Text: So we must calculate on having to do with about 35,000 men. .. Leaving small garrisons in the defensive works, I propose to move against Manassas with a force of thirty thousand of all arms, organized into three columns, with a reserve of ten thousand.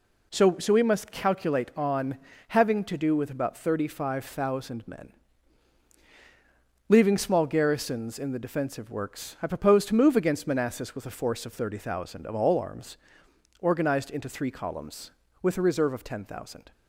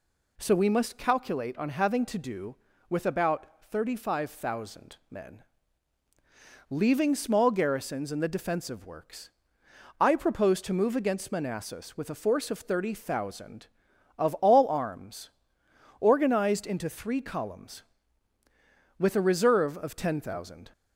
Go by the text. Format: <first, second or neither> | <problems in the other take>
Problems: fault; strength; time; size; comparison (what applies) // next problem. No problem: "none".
second | says "So" twice; at 0.5 s // pauses between "on" and "having"; slight; at 2.1 s; 0.32 s long